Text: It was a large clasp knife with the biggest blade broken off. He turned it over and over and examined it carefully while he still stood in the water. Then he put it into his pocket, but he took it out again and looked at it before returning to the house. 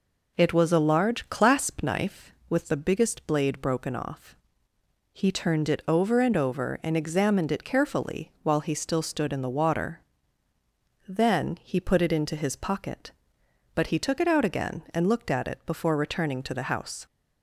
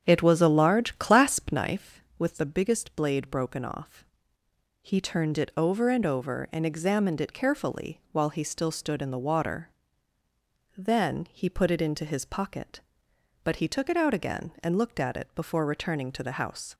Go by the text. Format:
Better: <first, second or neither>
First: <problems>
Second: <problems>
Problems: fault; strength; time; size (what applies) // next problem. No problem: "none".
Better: first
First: none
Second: starts louder than the rest; strong; until 1.7 s; 8 dB